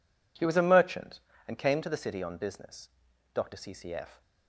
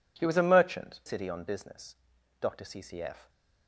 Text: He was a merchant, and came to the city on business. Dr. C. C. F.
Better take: first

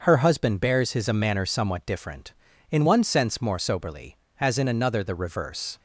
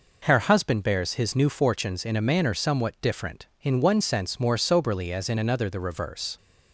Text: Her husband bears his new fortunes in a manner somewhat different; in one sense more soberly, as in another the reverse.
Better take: second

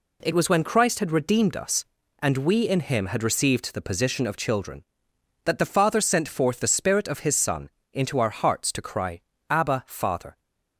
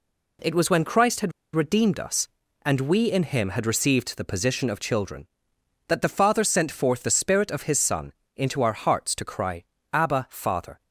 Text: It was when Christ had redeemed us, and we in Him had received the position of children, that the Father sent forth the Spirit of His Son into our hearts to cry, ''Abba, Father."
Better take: first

